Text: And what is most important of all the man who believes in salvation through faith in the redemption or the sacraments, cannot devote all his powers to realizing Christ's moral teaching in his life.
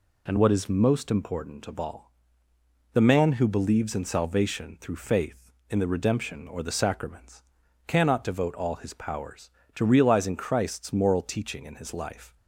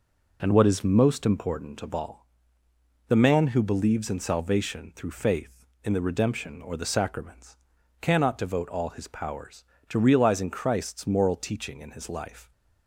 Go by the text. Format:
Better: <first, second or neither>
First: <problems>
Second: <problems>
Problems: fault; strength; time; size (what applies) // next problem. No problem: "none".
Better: first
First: pauses between "all" and "the"; noticeable; at 2.1 s; 0.82 s long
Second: starts louder than the rest; noticeable; until 2.2 s; 4.5 dB // pauses between "all" and "the"; noticeable; at 2.2 s; 0.82 s long